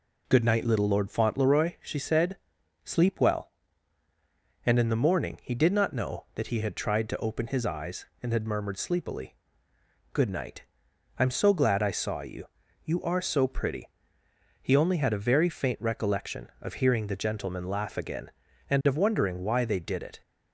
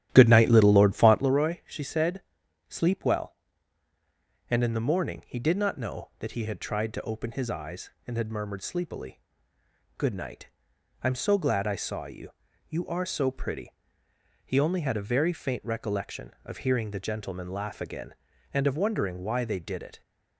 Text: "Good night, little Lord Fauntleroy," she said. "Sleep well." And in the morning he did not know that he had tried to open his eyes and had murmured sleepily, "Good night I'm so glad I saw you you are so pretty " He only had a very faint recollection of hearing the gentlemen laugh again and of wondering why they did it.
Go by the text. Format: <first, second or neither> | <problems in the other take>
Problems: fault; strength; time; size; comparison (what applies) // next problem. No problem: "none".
first | starts louder than the rest; strong; until 1.3 s; 12 dB // pauses between "night" and "I'm"; noticeable; at 10.4 s; 0.56 s long; noticeable in the first // pauses between "you" and "you"; slight; at 12.3 s; 0.36 s long; slight in the first